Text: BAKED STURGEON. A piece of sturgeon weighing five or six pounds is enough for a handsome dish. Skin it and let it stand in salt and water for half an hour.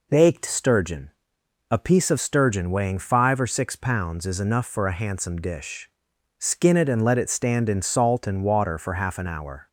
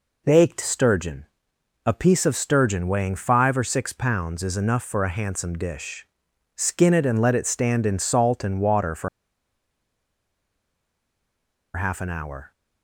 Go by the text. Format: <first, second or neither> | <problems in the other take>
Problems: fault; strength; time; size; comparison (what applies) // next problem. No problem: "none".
first | pauses between "for" and "half"; strong; at 9.0 s; 2.6 s long